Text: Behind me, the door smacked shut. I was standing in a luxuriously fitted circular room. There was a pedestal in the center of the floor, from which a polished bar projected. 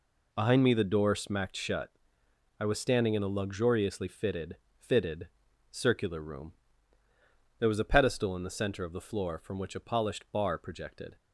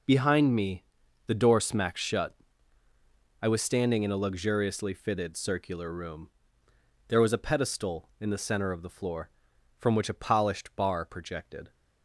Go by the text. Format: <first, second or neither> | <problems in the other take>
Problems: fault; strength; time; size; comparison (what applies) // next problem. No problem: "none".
second | says "fitted" twice; at 4.7 s